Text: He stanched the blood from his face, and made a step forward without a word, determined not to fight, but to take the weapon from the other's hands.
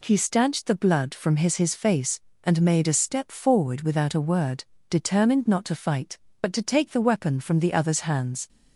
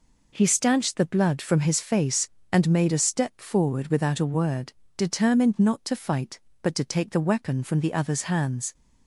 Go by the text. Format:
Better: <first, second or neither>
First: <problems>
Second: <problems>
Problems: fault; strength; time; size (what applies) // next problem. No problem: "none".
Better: second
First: says "his" twice; at 1.5 s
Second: none